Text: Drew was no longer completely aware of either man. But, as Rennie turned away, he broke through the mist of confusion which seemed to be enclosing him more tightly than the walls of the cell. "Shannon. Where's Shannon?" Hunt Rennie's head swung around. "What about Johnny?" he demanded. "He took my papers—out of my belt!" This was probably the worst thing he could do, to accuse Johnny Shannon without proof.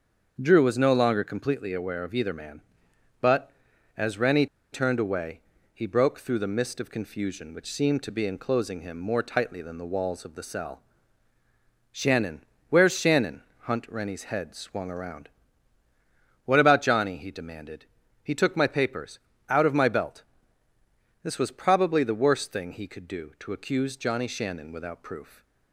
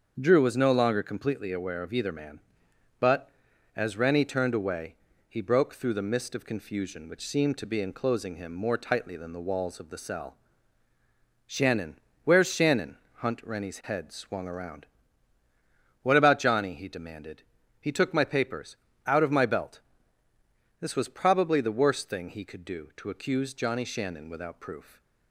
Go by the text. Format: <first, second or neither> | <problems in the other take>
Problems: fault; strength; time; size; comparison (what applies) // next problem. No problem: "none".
second | starts louder than the rest; until 1.4 s; 6.5 dB; also in the second // pauses between "Rennie" and "turned"; slight; at 4.4 s; 0.26 s long